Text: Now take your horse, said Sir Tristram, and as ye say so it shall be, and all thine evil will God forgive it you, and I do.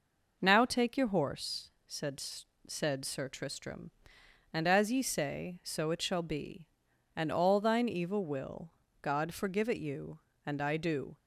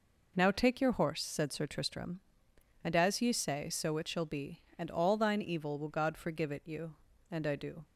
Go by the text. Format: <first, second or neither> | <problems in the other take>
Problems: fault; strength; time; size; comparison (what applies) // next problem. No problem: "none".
second | says "said" twice; at 2.6 s // pauses between "will" and "God"; slight; at 8.7 s; 0.30 s long